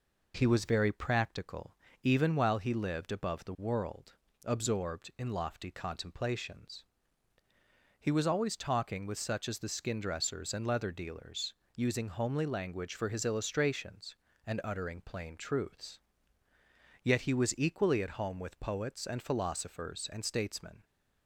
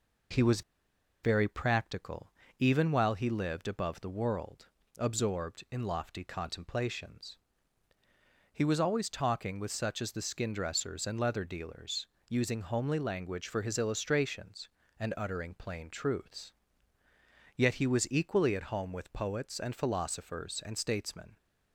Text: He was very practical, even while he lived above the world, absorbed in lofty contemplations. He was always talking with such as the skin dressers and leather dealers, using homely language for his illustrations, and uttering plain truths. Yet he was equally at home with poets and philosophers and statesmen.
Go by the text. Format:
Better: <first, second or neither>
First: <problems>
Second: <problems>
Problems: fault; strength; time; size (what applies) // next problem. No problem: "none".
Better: first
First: none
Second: pauses between "was" and "very"; noticeable; at 0.6 s; 0.61 s long